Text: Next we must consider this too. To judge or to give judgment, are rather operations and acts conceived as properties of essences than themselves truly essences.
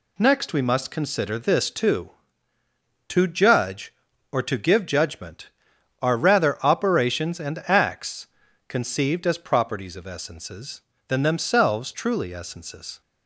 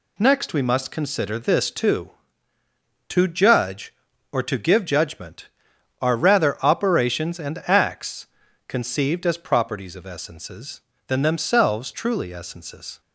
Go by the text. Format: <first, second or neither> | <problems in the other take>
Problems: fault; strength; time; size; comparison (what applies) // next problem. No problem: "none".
neither | pauses between "acts" and "conceived"; the same in both